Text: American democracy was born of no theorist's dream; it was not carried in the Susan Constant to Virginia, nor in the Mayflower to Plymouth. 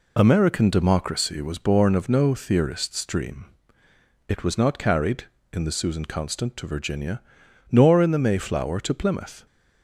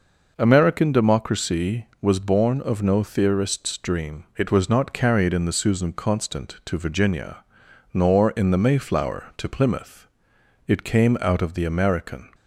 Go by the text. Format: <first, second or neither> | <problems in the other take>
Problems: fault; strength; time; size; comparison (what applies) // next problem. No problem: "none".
first | goes on to say "It came out of the American"; from 10.6 s on; 1.6 s long